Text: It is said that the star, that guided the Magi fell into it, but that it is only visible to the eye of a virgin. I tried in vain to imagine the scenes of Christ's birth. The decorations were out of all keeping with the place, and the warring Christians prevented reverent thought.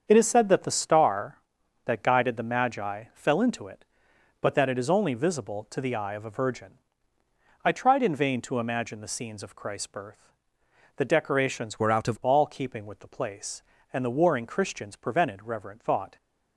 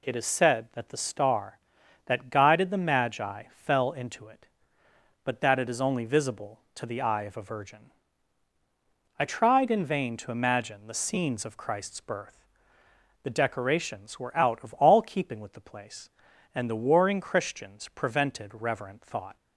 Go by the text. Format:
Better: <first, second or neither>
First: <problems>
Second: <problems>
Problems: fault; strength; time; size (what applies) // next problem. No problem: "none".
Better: second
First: starts louder than the rest; strong; until 1.0 s; 7 dB // changes voice from "were" to "of"; from 11.7 to 12.1 s; 0.4 s long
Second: none